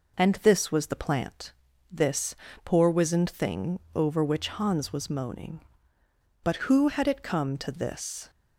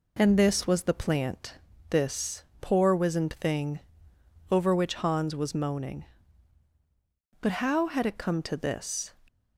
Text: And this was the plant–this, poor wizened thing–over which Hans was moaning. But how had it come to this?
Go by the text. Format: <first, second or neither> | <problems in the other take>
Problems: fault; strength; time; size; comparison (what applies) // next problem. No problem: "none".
second | says "who" for "how"; at 6.5 s